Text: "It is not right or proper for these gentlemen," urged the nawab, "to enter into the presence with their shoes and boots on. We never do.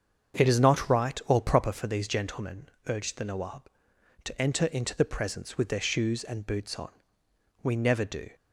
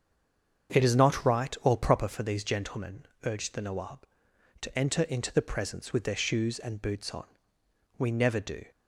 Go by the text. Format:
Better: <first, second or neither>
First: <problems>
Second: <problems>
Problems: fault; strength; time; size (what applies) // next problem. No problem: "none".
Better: first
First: starts louder than the rest; strong; until 1.4 s; 7 dB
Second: stays silent before the first word; slight; until 0.6 s; 0.6 s long // starts louder than the rest; strong; until 1.8 s; 7 dB